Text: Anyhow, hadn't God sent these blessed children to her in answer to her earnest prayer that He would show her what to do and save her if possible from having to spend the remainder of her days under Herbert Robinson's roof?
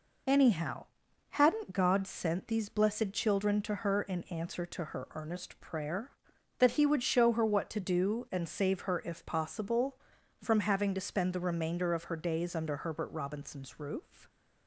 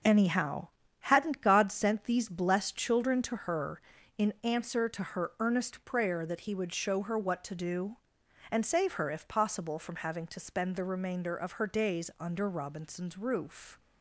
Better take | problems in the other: first | skips "Herbert"; at 12.4 s

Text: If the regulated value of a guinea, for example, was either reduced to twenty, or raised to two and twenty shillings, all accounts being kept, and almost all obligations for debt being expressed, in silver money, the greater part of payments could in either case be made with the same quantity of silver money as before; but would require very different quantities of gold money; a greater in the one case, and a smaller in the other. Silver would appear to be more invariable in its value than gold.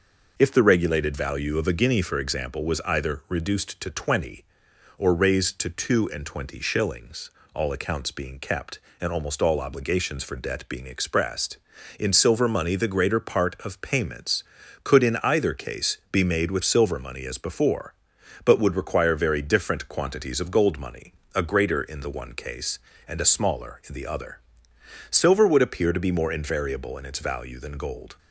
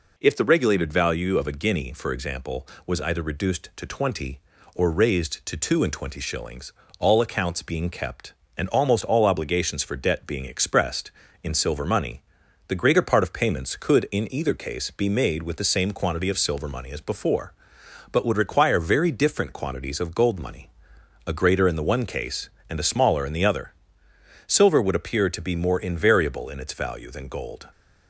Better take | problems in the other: second | skips "the same quantity of"; at 16.6 s

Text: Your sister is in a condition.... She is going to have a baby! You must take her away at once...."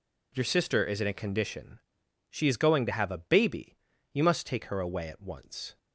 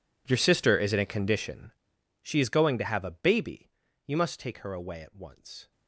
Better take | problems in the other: first | gets quieter; strong; throughout; 22 dB

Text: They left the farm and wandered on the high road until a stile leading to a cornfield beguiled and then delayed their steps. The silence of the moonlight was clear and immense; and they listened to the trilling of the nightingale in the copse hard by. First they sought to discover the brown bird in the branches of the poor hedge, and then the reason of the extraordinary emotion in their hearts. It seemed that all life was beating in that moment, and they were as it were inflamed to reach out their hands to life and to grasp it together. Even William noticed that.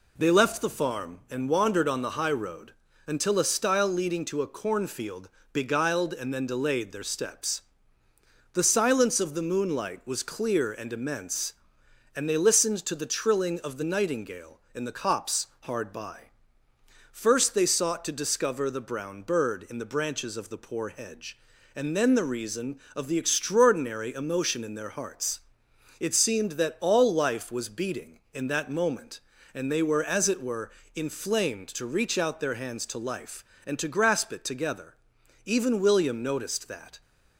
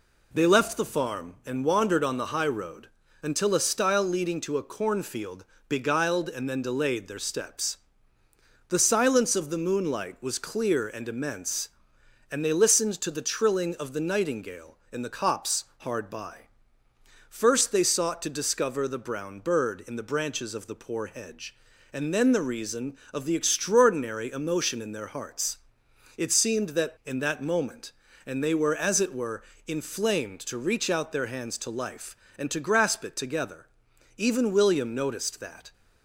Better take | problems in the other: first | pauses between "road" and "until"; slight; at 2.8 s; 0.34 s long; slight in the first // pauses between "cornfield" and "beguiled"; slight; at 5.4 s; 0.24 s long; slight in the first // pauses between "copse" and "hard"; slight; at 15.6 s; 0.16 s long; slight in the first // skips "all life was beating"; at 26.9 s // pauses between "were" and "inflamed"; slight; at 29.4 s; 0.26 s long; slight in the first

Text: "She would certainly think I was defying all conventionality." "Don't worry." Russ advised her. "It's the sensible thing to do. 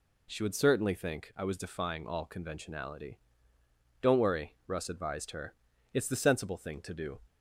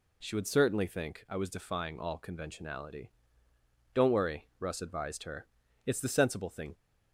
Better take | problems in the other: first | stops before "to do"; at 6.7 s

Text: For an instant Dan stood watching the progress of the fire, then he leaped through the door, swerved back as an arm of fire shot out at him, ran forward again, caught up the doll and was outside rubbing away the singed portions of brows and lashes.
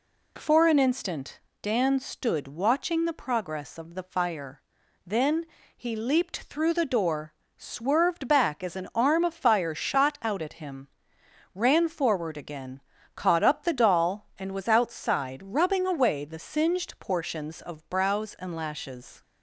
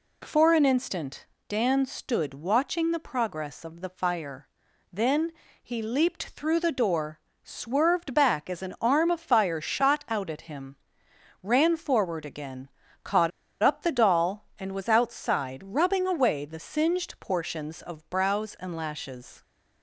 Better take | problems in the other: first | pauses between "instant" and "Dan"; slight; at 1.2 s; 0.24 s long; slight in the first // pauses between "then" and "he"; slight; at 5.3 s; 0.28 s long; slight in the first // pauses between "caught" and "up"; slight; at 13.3 s; 0.33 s long

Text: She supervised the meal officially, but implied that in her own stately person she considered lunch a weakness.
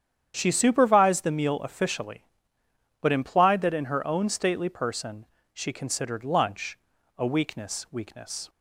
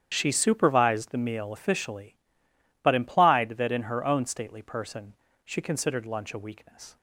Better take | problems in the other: second | starts louder than the rest; strong; until 1.3 s; 9 dB; strong in the second // pauses between "person" and "she"; slight; at 5.2 s; 0.26 s long; slight in the second // pauses between "lunch" and "a"; at 6.7 s; 0.40 s long // says "weakness" twice; at 7.8 s

